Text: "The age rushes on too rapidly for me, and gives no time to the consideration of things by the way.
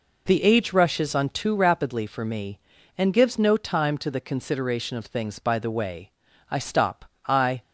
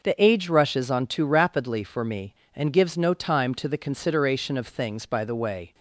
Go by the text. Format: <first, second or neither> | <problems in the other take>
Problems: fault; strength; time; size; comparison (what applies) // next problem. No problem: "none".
second | goes on to say "I stop I"; noticeable; from 6.5 s on; 1.1 s long